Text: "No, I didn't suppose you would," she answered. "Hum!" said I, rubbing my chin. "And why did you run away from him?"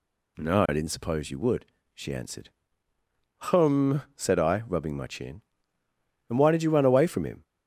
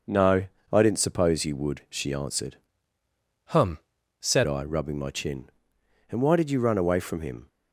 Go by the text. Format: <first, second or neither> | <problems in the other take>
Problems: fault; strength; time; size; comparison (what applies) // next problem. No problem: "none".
first | changes voice from "Hum" to "said"; from 3.4 to 4.4 s; 1.0 s long